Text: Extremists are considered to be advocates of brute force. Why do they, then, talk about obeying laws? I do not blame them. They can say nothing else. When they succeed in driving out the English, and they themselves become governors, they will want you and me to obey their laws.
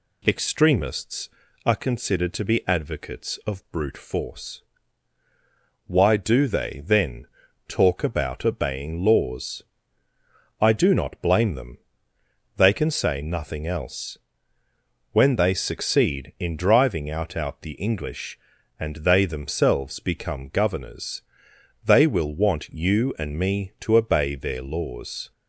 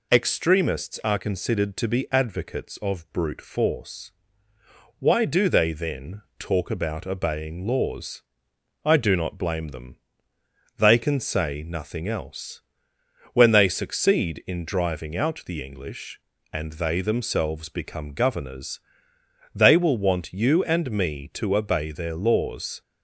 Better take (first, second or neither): second